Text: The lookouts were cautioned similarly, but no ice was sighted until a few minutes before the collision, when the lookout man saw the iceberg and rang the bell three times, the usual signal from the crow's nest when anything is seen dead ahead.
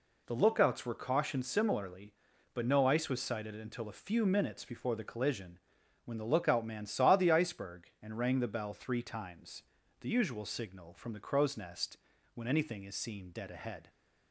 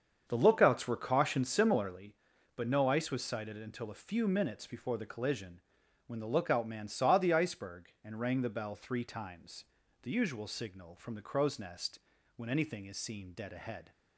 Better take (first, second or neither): first